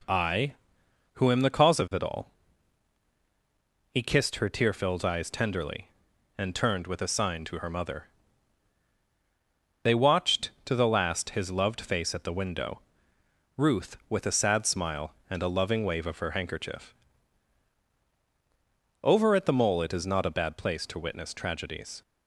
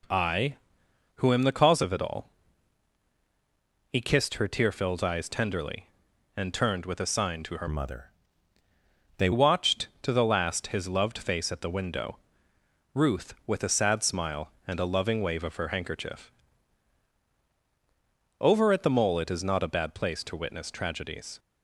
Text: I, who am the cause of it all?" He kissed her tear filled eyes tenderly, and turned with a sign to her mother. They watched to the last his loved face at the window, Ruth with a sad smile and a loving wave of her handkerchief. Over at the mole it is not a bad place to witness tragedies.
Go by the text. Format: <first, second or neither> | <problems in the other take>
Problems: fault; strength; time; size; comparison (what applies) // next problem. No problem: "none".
first | changes voice from "mother" to "They"; from 7.6 to 9.2 s; 1.6 s long